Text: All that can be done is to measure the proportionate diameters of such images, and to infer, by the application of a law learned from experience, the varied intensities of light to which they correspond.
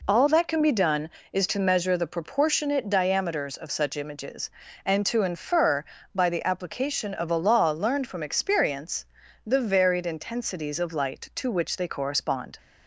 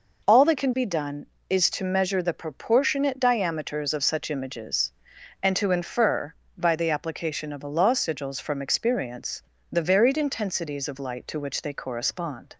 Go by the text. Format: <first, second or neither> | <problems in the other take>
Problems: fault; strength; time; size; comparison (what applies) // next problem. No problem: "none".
first | says "sigils" for "learned"; at 7.9 s